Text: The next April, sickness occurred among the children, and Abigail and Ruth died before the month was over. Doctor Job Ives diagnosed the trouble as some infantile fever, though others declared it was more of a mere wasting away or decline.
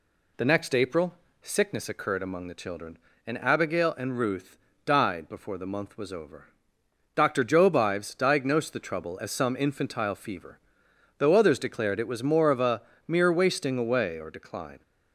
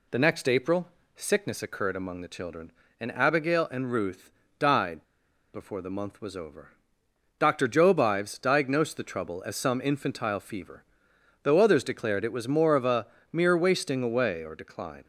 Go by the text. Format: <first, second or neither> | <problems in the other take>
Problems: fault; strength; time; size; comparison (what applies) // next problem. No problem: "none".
first | pauses between "Ruth" and "died"; slight; at 4.3 s; 0.26 s long; slight in the first // pauses between "died" and "before"; noticeable; at 5.0 s; 0.49 s long // pauses between "a" and "mere"; slight; at 13.0 s; 0.26 s long; slight in the first